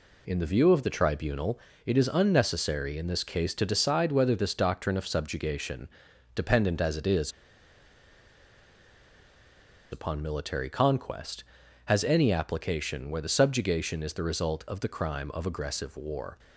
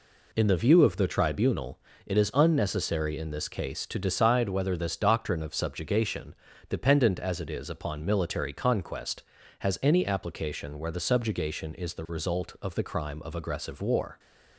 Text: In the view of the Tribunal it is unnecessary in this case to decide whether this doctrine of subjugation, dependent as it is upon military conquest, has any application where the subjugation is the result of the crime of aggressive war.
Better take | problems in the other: second | pauses between "Tribunal" and "it"; slight; at 1.5 s; 0.26 s long; slight in the second // pauses between "is" and "upon"; strong; at 7.2 s; 2.6 s long

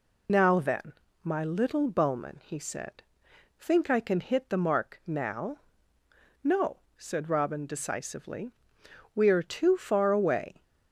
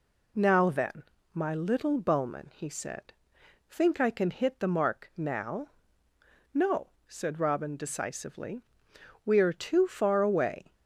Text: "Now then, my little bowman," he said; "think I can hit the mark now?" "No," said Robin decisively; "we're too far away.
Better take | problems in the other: second | loses the start of "Now"; at 0.2 s; 50 ms

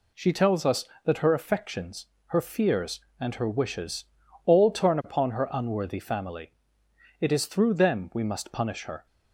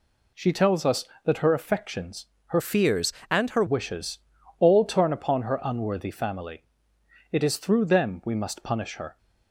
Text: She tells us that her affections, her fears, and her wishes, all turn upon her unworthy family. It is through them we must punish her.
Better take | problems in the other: first | changes voice from "fears" to "her"; from 2.5 to 3.6 s; 1.1 s long

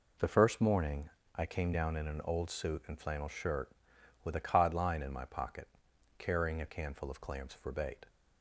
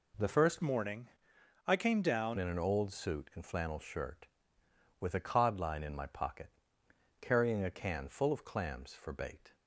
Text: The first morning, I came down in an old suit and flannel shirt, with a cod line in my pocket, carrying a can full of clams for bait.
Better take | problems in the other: first | changes voice from "morning" to "down"; from 0.6 to 2.3 s; 1.7 s long

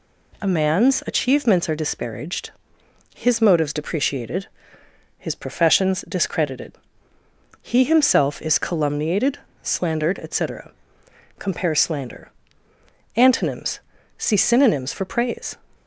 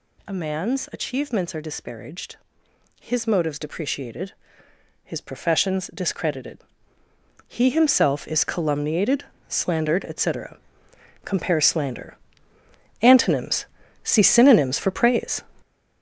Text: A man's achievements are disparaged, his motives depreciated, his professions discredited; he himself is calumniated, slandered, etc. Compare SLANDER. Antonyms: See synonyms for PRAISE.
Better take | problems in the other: first | gets louder; strong; throughout; 8.5 dB

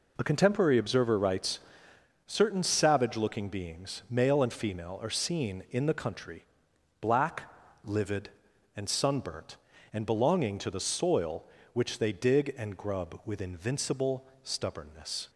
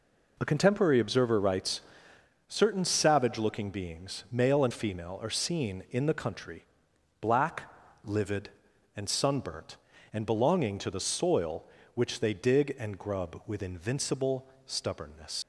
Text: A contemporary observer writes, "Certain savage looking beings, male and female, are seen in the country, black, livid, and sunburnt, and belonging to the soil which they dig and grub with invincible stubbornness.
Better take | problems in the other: first | pauses between "invincible" and "stubbornness"; slight; at 14.4 s; 0.20 s long; slight in the first // leaves "stubbornness" unfinished; at 15.4 s; 105 ms

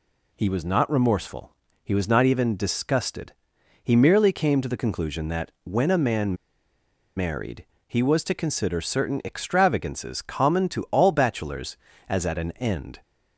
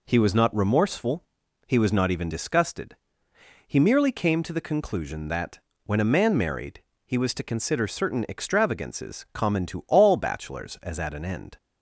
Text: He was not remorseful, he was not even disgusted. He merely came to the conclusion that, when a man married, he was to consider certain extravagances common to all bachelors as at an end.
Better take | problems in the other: second | pauses between "man" and "married"; noticeable; at 6.3 s; 0.80 s long

